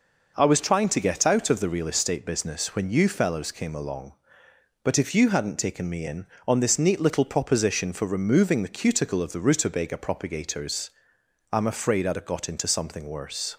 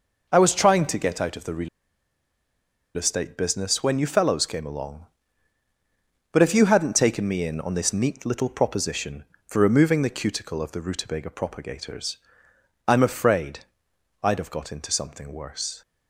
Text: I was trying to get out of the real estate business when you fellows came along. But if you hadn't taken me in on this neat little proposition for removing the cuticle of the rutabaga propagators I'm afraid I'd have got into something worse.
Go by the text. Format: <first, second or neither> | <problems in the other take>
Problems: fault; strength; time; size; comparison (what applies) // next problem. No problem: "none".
first | pauses between "real" and "estate"; strong; at 1.6 s; 1.2 s long // pauses between "propagators" and "I'm"; noticeable; at 12.1 s; 0.70 s long; noticeable in the first // pauses between "afraid" and "I'd"; noticeable; at 13.6 s; 0.58 s long